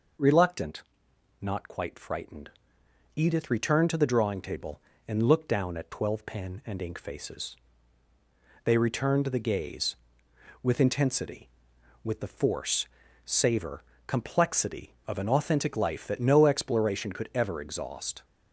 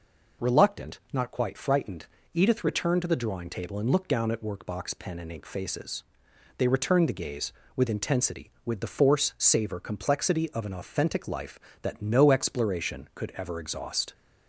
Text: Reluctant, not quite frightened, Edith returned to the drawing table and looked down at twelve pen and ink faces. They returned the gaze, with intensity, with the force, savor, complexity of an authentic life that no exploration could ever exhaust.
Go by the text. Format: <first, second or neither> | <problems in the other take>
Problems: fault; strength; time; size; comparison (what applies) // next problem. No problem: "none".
first | says "workbox" for "twelve"; at 4.4 s